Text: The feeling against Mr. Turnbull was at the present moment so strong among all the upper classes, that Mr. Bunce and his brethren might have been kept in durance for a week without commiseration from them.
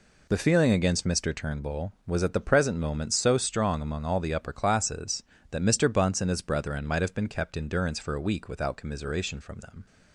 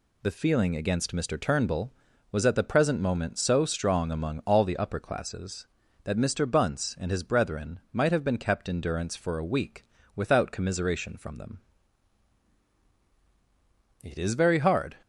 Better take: first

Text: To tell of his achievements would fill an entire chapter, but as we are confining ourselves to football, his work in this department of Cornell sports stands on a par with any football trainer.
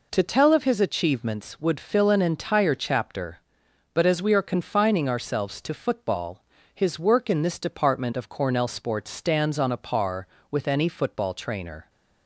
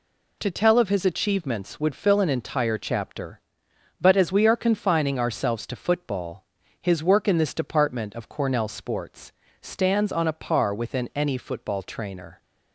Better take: first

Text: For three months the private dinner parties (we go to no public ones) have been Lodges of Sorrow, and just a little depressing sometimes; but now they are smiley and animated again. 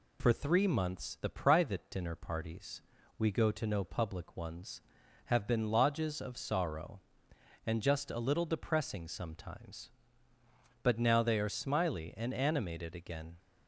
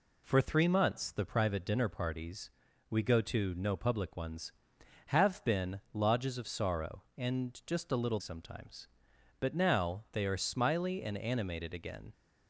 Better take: first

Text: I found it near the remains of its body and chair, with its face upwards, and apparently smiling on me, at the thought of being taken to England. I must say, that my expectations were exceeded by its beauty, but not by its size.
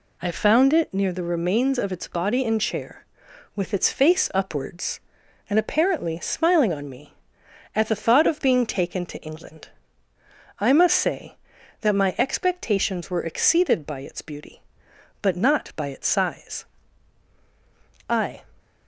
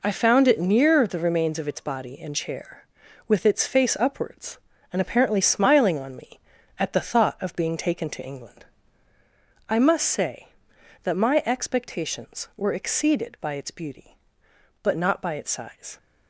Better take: second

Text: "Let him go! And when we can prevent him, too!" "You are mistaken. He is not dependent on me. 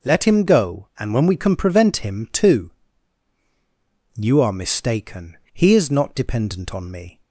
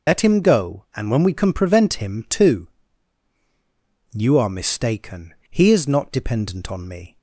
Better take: first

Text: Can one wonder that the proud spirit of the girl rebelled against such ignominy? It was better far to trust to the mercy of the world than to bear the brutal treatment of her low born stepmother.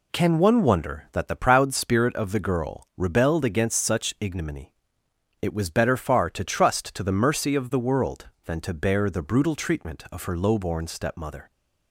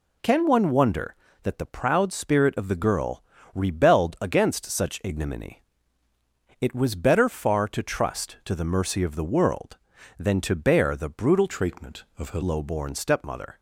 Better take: first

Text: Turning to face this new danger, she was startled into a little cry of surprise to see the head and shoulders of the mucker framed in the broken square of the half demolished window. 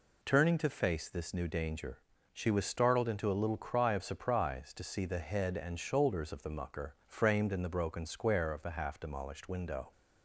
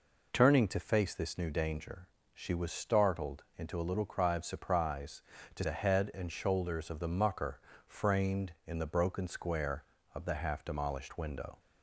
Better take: first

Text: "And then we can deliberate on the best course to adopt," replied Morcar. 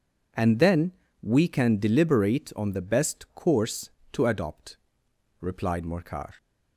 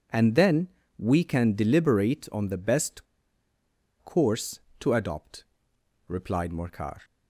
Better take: first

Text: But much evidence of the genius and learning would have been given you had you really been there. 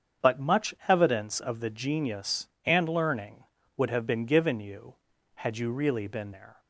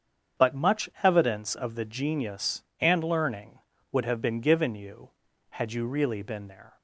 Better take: neither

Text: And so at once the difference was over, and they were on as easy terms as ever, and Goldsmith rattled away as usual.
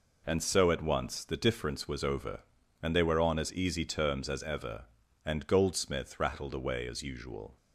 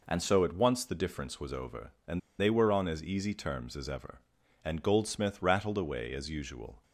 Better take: first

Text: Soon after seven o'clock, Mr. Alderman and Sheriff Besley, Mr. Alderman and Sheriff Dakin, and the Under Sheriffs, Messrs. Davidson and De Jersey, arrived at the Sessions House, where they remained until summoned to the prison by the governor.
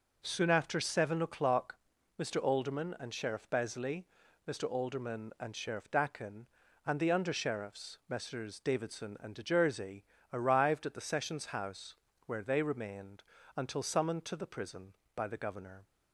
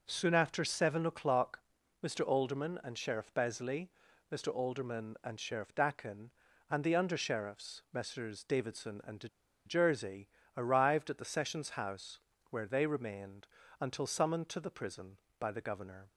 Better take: first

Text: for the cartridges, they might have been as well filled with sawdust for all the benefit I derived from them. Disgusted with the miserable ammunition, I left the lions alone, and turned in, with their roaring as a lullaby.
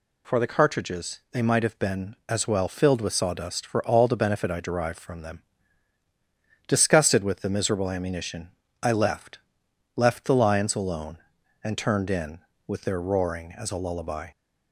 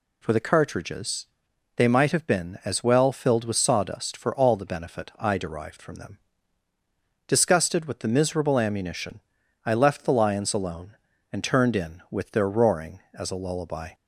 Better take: second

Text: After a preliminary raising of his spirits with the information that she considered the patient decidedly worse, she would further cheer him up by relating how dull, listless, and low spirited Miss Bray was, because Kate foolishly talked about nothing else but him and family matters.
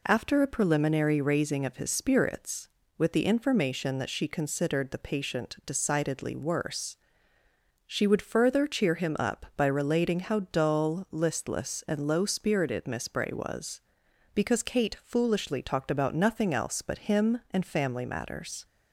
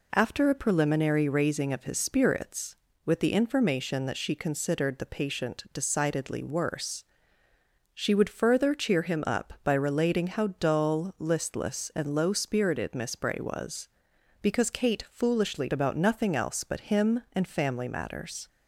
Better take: first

